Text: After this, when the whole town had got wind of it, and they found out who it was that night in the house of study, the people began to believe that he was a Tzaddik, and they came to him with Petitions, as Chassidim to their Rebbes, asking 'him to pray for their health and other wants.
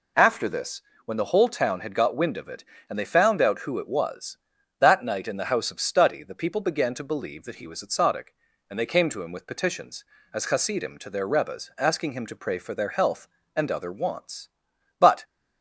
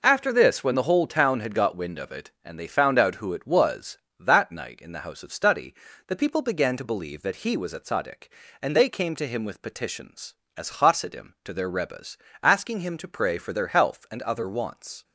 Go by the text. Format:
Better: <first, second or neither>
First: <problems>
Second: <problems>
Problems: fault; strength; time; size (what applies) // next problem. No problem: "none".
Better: second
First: goes on to say "But"; slight; from 14.9 s on; 0.24 s long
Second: none